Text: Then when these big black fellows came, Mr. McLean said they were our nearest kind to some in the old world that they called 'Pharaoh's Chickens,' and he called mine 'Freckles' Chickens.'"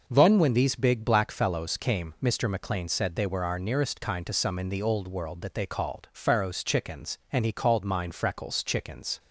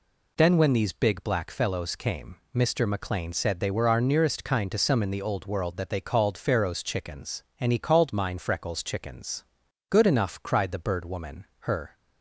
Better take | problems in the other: first | goes on to say "Good enough cried the Bird Woman her"; strong; from 9.9 s on; 2.0 s long

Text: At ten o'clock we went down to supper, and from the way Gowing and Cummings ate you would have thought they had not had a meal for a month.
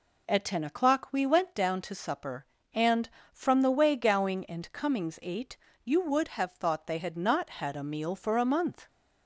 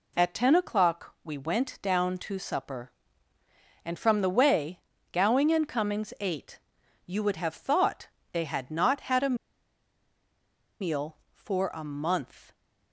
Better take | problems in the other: first | pauses between "way" and "Gowing"; slight; at 4.7 s; 0.32 s long // pauses between "ate" and "you"; at 6.6 s; 0.44 s long; slight in the first // pauses between "thought" and "they"; slight; at 8.0 s; 0.24 s long // pauses between "a" and "meal"; strong; at 9.3 s; 1.4 s long

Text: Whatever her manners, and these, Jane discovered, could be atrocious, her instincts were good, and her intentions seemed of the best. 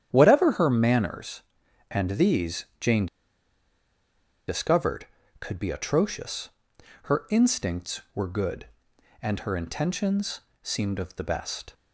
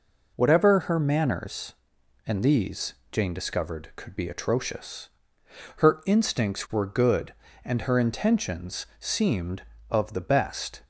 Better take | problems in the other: second | starts louder than the rest; strong; until 1.1 s; 9.5 dB // pauses between "Jane" and "discovered"; strong; at 3.0 s; 1.4 s long // pauses between "intentions" and "seemed"; slight; at 10.3 s; 0.24 s long

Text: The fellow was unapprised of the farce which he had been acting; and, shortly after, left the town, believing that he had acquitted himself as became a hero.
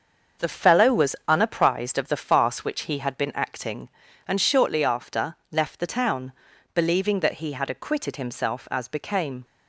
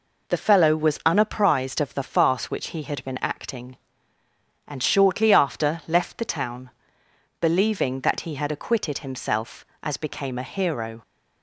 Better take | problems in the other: second | starts louder than the rest; until 1.5 s; 6.5 dB // stops before "a hero"; at 9.4 s

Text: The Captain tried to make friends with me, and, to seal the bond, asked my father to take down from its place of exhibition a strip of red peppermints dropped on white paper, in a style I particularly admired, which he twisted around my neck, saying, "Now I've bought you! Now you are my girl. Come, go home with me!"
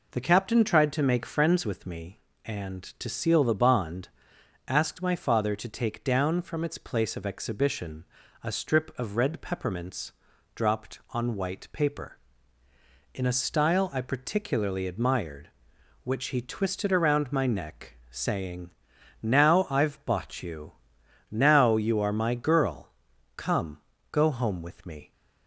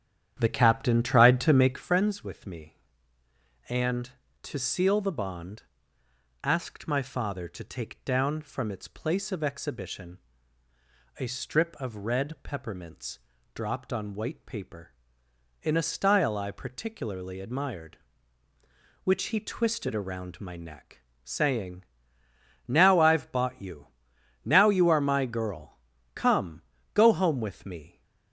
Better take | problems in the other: first | starts louder than the rest; strong; until 1.9 s; 9.5 dB // pauses between "exhibition" and "a"; at 10.1 s; 1.0 s long; also in the first // pauses between "peppermints" and "dropped"; at 13.1 s; 0.38 s long; also in the first

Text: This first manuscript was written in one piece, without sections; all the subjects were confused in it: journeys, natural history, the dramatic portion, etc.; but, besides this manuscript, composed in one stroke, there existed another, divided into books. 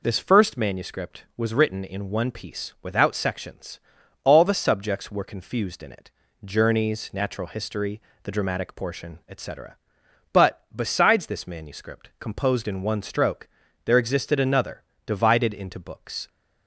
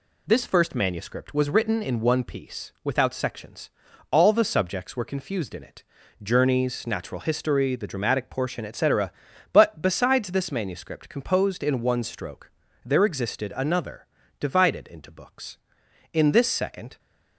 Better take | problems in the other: first | goes on to say "In this second"; noticeable; from 16.1 s on; 0.86 s long

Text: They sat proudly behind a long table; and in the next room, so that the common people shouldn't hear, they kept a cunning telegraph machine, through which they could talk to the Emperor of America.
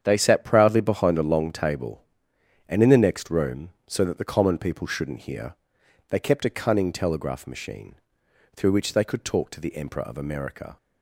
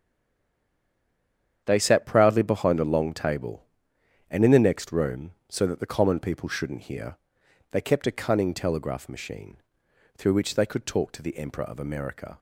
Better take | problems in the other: first | stays silent before the first word; noticeable; until 1.6 s; 1.6 s long // starts louder than the rest; strong; until 2.6 s; 8 dB; strong in the first

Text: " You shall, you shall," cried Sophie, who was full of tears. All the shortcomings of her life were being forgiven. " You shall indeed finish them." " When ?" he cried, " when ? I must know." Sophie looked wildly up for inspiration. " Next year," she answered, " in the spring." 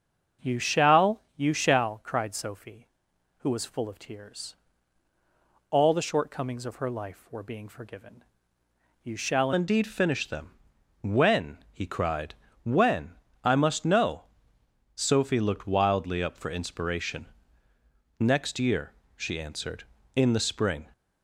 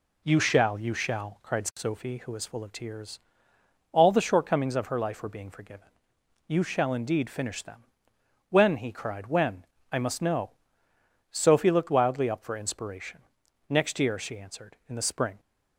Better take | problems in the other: second | starts louder than the rest; strong; until 1.5 s; 8 dB // changes voice at "indeed"; from 9.5 s on; 11.3 s long

